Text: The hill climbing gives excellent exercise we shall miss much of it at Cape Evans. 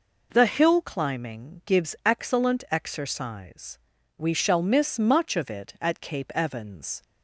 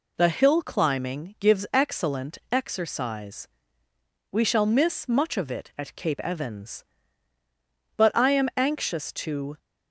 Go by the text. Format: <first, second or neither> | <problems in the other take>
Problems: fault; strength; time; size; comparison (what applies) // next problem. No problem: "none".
first | pauses between "exercise" and "we"; noticeable; at 3.4 s; 0.84 s long; also in the first // goes on to say "But I am anxious to"; from 7.9 s on; 1.6 s long